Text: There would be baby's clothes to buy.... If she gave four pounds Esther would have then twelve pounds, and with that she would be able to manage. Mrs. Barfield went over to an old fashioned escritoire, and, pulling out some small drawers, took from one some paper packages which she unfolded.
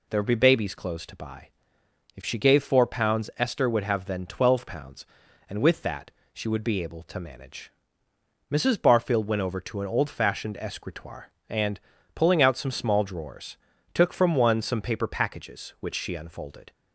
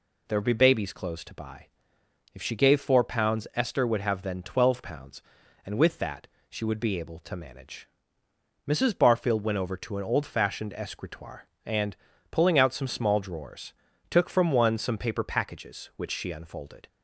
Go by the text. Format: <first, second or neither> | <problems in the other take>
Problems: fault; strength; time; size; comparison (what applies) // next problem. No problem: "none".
neither | pauses between "that" and "she"; slight; the same in both